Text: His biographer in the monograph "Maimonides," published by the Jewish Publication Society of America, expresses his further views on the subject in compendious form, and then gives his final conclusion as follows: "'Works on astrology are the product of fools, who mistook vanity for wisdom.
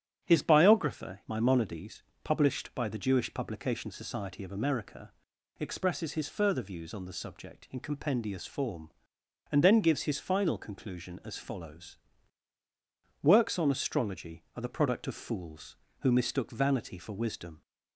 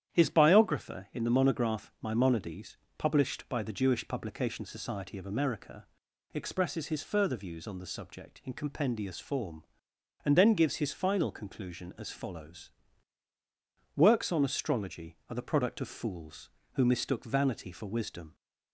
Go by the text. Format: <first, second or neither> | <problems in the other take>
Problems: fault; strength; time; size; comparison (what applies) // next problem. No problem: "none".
second | starts louder than the rest; strong; until 1.3 s; 9.5 dB; strong in the second // skips "in the monograph"; at 1.2 s